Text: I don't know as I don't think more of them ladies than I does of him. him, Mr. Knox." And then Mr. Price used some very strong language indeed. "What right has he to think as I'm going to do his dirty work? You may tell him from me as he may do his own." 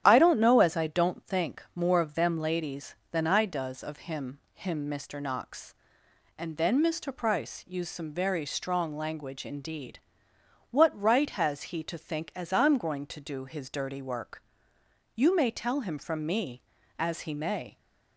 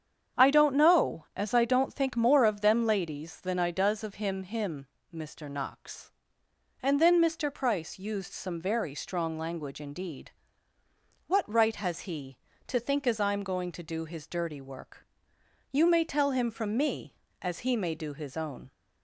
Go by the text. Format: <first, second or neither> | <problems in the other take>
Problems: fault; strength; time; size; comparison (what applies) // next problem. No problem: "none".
second | starts louder than the rest; strong; until 1.0 s; 10.5 dB; strong in the second // stops before "do his own"; at 17.7 s